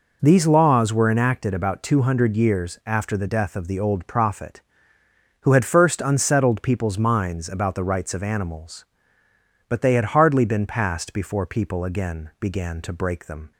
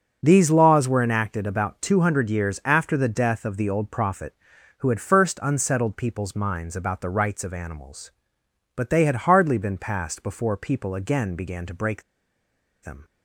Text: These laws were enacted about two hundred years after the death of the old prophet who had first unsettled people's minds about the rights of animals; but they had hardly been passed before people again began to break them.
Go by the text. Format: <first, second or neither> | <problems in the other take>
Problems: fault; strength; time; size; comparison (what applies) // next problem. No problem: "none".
first | pauses between "break" and "them"; noticeable; at 12.0 s; 0.81 s long